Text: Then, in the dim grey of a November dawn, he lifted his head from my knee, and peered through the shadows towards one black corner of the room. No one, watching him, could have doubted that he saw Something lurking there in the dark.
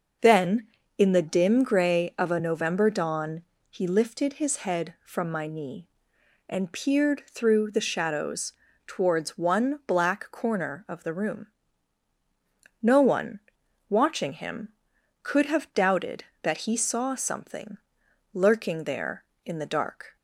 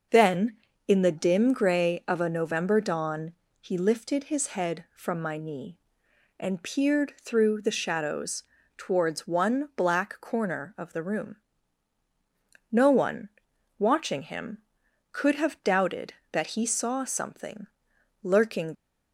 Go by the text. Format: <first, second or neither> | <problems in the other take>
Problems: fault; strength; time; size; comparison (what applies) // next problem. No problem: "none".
first | starts louder than the rest; noticeable; until 1.4 s; 6 dB; also in the first // pauses between "shadows" and "towards"; slight; at 8.4 s; 0.34 s long; slight in the first // pauses between "Something" and "lurking"; noticeable; at 17.6 s; 0.54 s long; noticeable in the first // stops before "there in the dark"; at 18.7 s